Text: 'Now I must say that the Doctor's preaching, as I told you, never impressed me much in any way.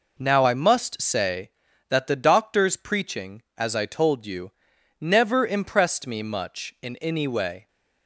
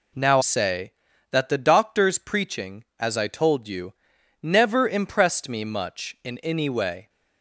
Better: first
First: none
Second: skips "I must"; at 0.4 s

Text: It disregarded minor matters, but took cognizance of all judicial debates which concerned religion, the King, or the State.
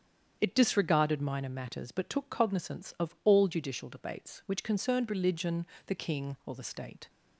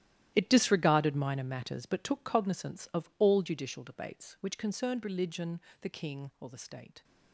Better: first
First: starts louder than the rest; strong; until 1.4 s; 8 dB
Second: gets quieter; strong; throughout; 14.5 dB // starts louder than the rest; strong; until 1.3 s; 13 dB

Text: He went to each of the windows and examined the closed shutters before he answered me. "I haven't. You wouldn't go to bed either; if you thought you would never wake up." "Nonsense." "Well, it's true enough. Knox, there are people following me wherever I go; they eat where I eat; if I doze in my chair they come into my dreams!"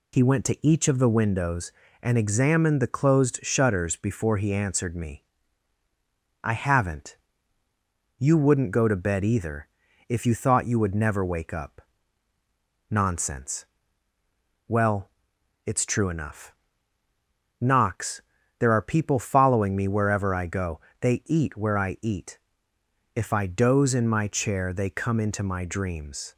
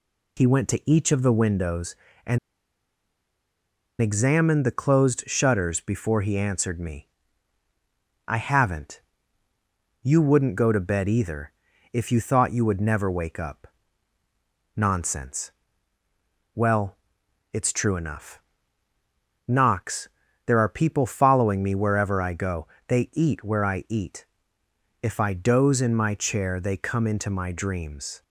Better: first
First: none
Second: pauses between "and" and "examined"; strong; at 2.3 s; 1.6 s long

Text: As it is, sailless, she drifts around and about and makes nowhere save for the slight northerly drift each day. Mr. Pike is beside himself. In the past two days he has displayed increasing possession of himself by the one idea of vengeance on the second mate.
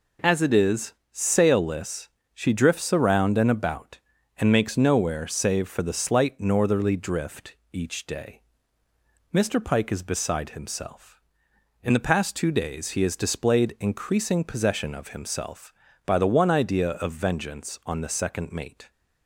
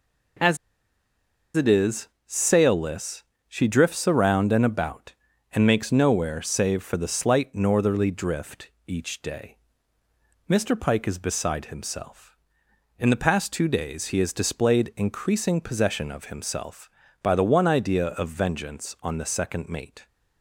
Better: first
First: pauses between "drift" and "each"; slight; at 7.5 s; 0.16 s long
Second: pauses between "As" and "it"; at 0.5 s; 0.99 s long // pauses between "drift" and "each"; slight; at 8.7 s; 0.16 s long

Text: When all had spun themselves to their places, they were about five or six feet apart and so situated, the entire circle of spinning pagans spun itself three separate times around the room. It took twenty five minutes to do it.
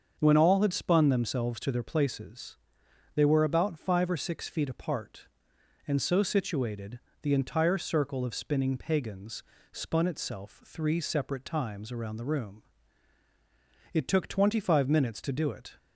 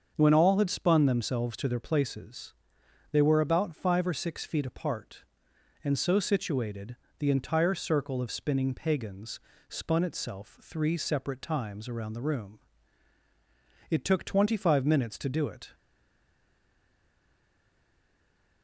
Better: first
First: starts louder than the rest; until 1.2 s; 7 dB // pauses between "pagans" and "spun"; slight; at 9.4 s; 0.30 s long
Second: starts louder than the rest; until 1.1 s; 7 dB // pauses between "pagans" and "spun"; slight; at 9.3 s; 0.30 s long // stays silent after the last word; strong; from 15.7 s on; 2.9 s long

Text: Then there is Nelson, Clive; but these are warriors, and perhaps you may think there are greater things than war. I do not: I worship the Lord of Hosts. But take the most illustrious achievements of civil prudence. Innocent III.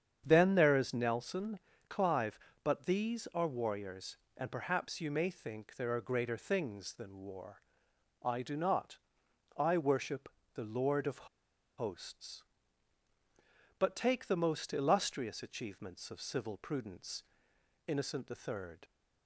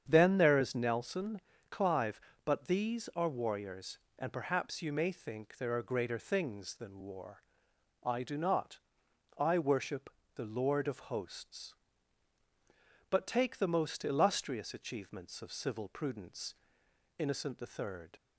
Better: second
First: starts louder than the rest; strong; until 1.2 s; 8 dB // pauses between "worship" and "the"; slight; at 10.3 s; 0.24 s long // pauses between "of" and "Hosts"; noticeable; at 11.2 s; 0.50 s long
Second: starts louder than the rest; strong; until 1.1 s; 8 dB // pauses between "worship" and "the"; slight; at 10.1 s; 0.24 s long

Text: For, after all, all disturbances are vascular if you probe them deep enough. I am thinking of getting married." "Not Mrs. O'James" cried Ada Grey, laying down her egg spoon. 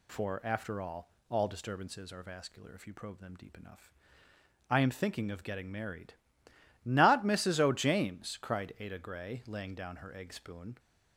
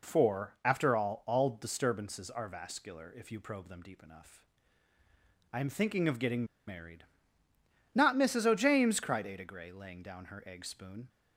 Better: first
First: none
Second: pauses between "getting" and "married"; slight; at 6.4 s; 0.23 s long

